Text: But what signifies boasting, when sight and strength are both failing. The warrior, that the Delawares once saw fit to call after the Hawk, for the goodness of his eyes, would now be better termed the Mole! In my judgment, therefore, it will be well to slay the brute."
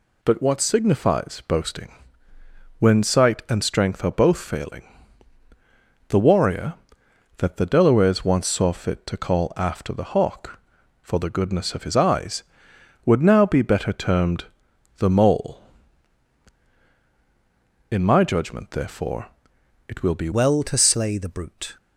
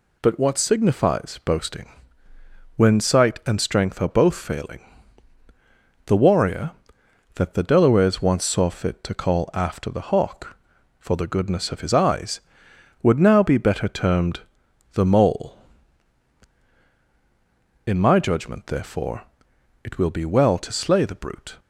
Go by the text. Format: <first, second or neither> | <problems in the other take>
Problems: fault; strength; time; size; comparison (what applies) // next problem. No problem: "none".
second | pauses between "termed" and "the"; noticeable; at 14.4 s; 0.52 s long; noticeable in the second // changes voice at "well"; from 20.3 s on; 1.4 s long